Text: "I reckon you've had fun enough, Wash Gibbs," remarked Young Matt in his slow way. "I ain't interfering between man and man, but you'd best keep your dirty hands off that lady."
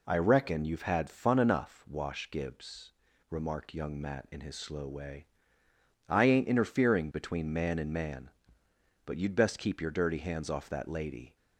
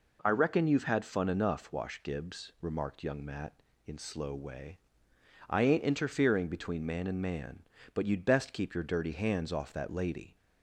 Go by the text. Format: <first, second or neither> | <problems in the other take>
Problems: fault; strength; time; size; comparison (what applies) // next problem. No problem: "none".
first | skips "his"; at 3.9 s